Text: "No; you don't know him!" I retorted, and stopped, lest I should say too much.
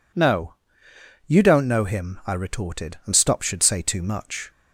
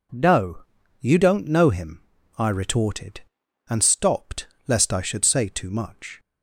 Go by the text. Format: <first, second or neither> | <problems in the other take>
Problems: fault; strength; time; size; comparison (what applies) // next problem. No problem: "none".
second | skips "lest I"; at 3.4 s